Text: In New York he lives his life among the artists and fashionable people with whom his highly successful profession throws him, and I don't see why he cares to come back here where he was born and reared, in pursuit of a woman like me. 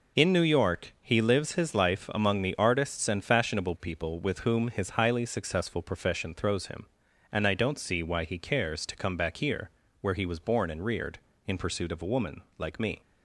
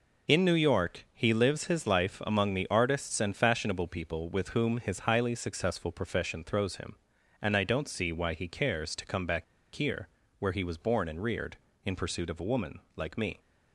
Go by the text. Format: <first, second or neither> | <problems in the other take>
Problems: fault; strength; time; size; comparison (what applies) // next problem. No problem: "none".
first | pauses between "back" and "here"; slight; at 9.4 s; 0.30 s long // pauses between "here" and "where"; slight; at 10.0 s; 0.30 s long; slight in the first // pauses between "woman" and "like"; slight; at 12.7 s; 0.18 s long; slight in the first